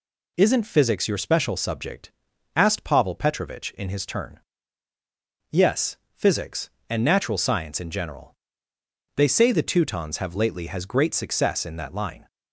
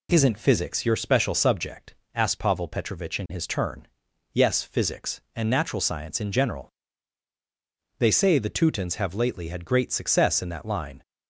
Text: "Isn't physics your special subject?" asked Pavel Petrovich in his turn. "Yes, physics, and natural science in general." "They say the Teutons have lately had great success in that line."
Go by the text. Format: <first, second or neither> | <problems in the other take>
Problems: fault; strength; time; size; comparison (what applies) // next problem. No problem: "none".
second | says "has" for "had"; at 10.6 s